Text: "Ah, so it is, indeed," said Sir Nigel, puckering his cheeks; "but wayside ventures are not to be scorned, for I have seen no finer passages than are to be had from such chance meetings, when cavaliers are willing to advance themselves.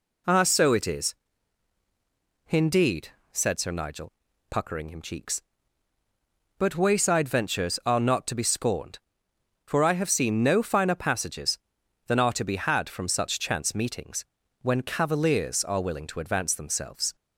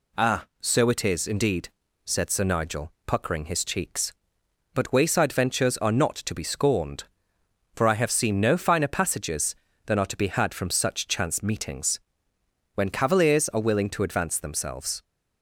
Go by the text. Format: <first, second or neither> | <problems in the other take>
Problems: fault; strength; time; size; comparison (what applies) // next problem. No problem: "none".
second | says "him" for "his"; at 4.8 s